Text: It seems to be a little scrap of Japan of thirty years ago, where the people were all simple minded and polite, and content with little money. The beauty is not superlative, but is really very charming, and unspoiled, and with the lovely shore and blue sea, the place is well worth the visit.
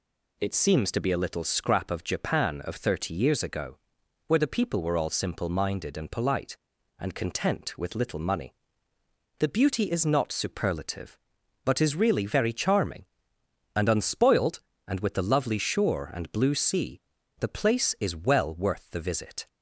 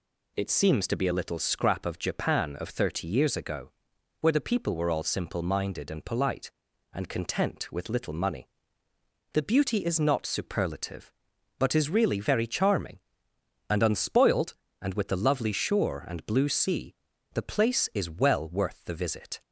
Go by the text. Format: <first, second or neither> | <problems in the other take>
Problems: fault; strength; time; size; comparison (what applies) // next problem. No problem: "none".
neither | none